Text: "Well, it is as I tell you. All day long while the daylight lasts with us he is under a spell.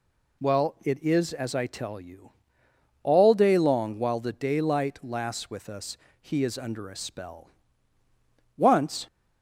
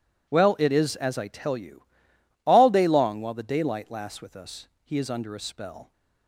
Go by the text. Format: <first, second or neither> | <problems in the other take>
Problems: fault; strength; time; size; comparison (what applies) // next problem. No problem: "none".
second | pauses between "us" and "he"; slight; at 5.9 s; 0.24 s long; slight in the second // goes on to say "Once"; from 8.5 s on; 0.50 s long